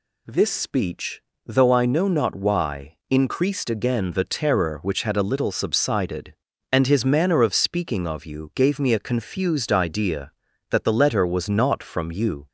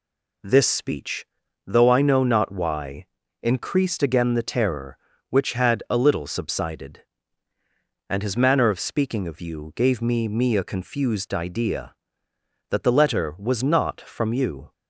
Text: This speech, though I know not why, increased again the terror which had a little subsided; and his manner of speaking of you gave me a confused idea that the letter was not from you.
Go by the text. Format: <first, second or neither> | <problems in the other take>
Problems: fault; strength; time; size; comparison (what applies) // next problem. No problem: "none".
first | says "me" twice; at 10.2 s